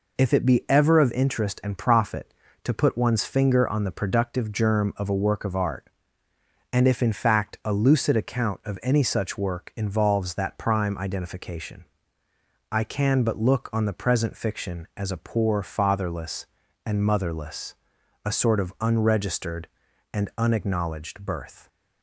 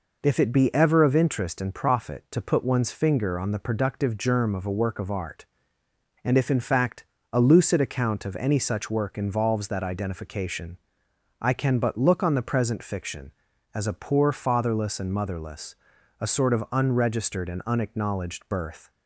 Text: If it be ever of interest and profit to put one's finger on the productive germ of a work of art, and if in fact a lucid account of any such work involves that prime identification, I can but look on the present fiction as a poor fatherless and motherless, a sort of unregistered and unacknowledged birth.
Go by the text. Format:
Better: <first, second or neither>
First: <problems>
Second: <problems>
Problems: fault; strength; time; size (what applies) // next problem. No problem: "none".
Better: first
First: none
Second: pauses between "fact" and "a"; slight; at 7.0 s; 0.26 s long // skips "prime"; at 9.8 s